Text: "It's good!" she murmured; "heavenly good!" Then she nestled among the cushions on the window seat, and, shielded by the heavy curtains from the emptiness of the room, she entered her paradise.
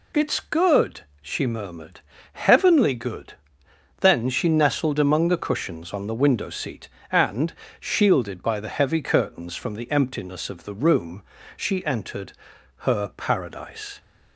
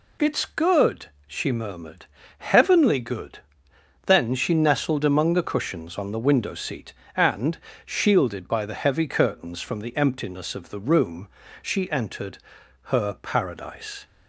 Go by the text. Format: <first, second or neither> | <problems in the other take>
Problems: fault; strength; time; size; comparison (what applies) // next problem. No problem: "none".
neither | pauses between "entered" and "her"; noticeable; the same in both